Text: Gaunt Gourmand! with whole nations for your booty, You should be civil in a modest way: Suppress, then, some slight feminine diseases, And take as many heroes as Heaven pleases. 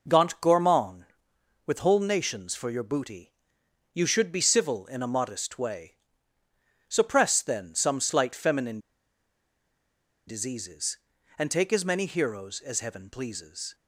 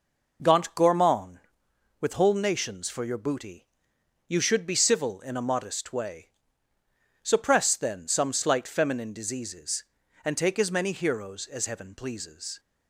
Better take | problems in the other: second | pauses between "feminine" and "diseases"; strong; at 8.7 s; 1.4 s long

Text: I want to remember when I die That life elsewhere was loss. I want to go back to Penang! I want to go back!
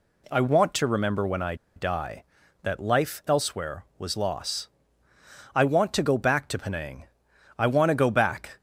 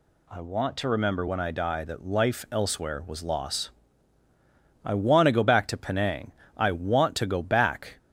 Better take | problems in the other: second | pauses between "I" and "die"; slight; at 1.5 s; 0.21 s long

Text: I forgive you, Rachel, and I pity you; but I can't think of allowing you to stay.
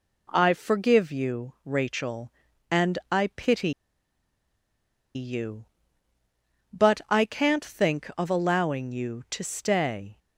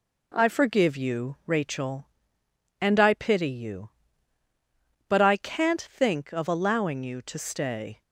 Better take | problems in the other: second | pauses between "pity" and "you"; strong; at 3.7 s; 1.4 s long

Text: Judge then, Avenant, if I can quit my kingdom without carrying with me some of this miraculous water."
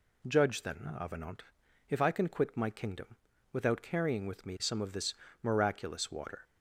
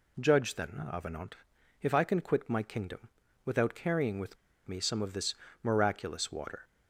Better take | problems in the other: first | pauses between "kingdom" and "without"; slight; at 3.0 s; 0.36 s long; slight in the first // pauses between "with" and "me"; slight; at 4.3 s; 0.31 s long // pauses between "this" and "miraculous"; slight; at 5.3 s; 0.30 s long; slight in the first

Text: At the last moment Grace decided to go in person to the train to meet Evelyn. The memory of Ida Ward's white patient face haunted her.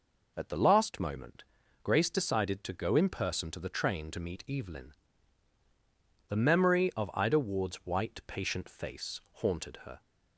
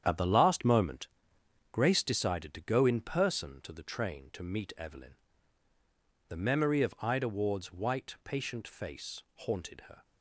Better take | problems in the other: first | gets quieter; strong; throughout; 9 dB // pauses between "moment" and "Grace"; noticeable; at 1.0 s; 0.66 s long; also in the first

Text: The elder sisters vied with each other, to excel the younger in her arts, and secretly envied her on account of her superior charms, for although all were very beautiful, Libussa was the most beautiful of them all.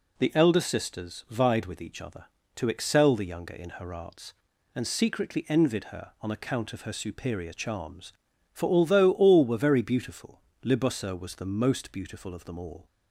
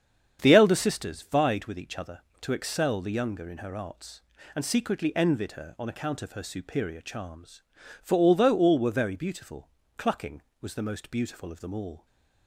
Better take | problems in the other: first | starts louder than the rest; strong; until 1.4 s; 8 dB // says "Clucking" for "Libussa"; at 9.9 s

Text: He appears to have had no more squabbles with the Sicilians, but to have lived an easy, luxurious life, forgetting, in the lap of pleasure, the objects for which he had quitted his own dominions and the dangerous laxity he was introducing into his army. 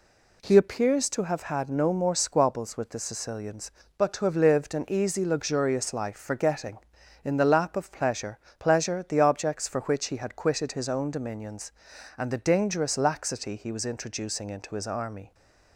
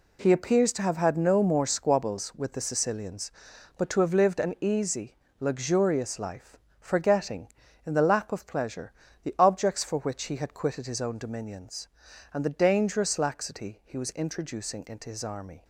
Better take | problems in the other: second | says "pleasure" twice; at 8.5 s

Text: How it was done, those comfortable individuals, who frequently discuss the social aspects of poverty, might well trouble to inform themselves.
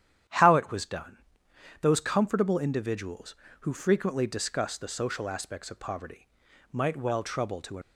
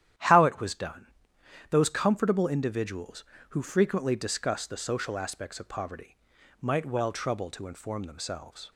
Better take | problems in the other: second | starts louder than the rest; strong; until 1.9 s; 10 dB; strong in the second // stops before "inform themselves"; at 7.8 s

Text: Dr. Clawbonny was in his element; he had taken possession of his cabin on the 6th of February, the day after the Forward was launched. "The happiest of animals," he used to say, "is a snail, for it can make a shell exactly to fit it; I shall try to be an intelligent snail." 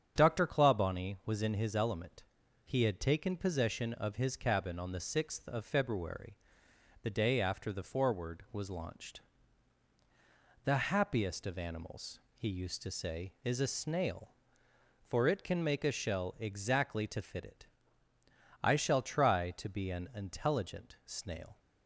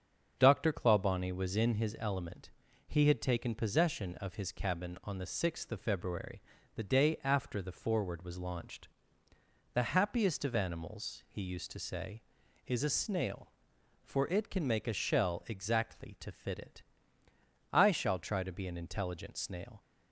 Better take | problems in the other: neither | starts louder than the rest; the same in both

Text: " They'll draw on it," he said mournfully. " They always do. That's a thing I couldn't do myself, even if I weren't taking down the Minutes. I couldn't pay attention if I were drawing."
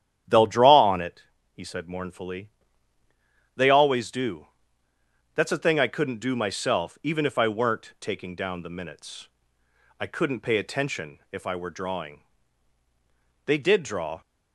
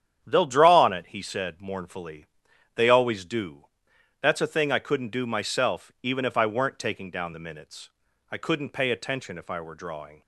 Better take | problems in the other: second | starts louder than the rest; strong; until 1.5 s; 9.5 dB; strong in the second // goes on to say "They did draw"; noticeable; from 13.4 s on; 0.76 s long

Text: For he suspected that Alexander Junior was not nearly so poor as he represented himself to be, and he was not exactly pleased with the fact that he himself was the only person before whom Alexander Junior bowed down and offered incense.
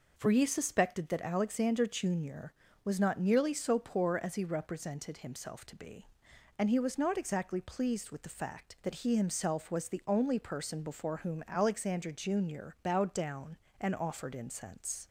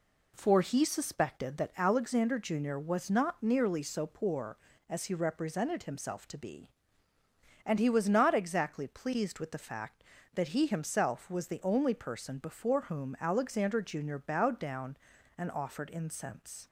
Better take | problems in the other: neither | none

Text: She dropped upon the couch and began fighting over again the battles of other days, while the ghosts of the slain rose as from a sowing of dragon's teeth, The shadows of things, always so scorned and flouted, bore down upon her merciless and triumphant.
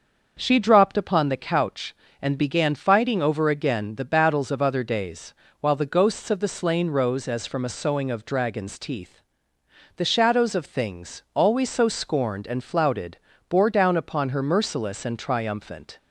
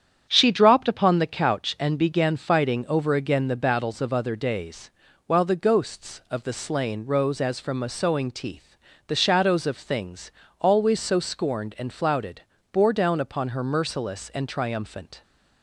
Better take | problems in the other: first | starts louder than the rest; strong; until 1.3 s; 9 dB; also in the first // skips "of dragon's"; at 8.2 s

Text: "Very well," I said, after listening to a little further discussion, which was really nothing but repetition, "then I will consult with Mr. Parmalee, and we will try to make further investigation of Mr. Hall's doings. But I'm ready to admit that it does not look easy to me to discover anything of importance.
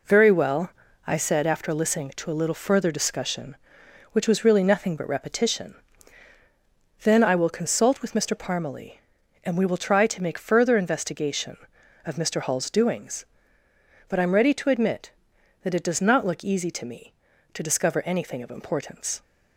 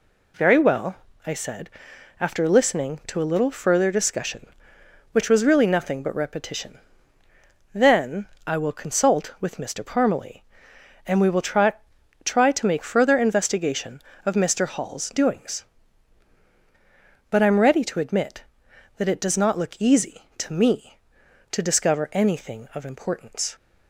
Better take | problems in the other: first | pauses between "then" and "I"; slight; at 8.2 s; 0.18 s long // says "try" twice; at 12.2 s

